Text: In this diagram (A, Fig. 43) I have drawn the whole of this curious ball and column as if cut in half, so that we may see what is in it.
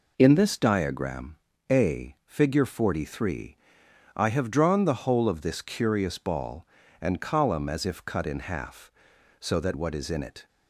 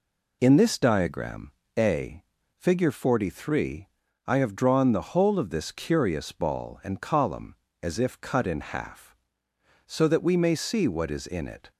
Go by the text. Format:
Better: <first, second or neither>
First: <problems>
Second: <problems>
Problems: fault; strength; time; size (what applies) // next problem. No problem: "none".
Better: second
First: skips "we may see"; at 9.7 s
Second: none